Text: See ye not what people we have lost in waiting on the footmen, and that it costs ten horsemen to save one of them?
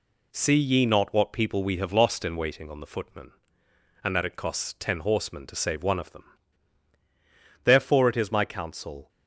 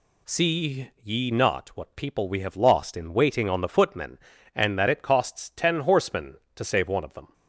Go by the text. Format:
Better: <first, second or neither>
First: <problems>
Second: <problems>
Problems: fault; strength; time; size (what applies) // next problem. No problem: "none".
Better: second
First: goes on to say "Therefore it is my counsel"; from 7.6 s on; 1.4 s long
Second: none